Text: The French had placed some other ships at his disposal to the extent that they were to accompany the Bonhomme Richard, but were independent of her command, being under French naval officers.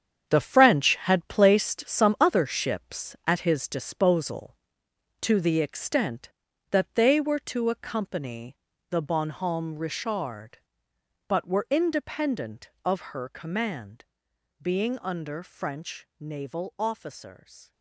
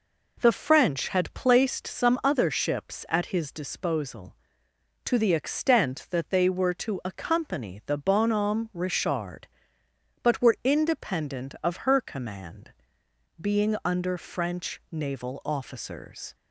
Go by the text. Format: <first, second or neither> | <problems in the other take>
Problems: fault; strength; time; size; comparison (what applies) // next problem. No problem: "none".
second | gets quieter; strong; throughout; 10 dB // pauses between "accompany" and "the"; slight; at 8.5 s; 0.32 s long